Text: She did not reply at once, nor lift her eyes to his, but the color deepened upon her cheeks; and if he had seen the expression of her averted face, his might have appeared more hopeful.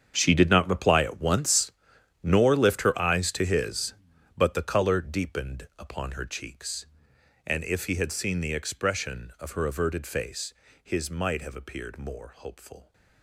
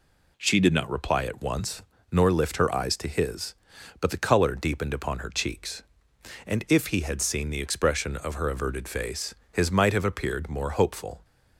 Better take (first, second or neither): second